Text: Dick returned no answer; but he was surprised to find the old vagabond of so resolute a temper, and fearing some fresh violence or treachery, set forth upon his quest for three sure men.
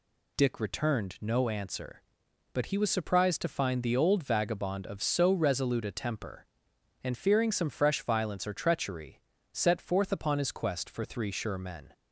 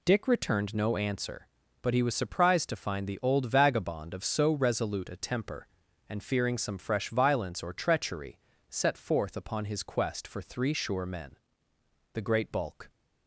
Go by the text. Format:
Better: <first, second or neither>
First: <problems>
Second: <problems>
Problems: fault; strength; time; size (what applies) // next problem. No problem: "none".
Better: first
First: none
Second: goes on to say "The great bulk"; noticeable; from 12.1 s on; 0.76 s long